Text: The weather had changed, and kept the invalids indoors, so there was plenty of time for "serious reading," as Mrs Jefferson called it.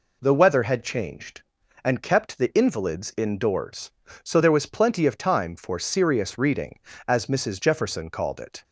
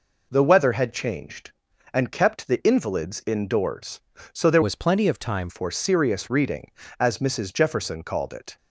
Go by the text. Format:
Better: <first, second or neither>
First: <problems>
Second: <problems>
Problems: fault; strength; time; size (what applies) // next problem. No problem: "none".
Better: first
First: none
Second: changes voice from "was" to "time"; from 4.6 to 5.4 s; 0.8 s long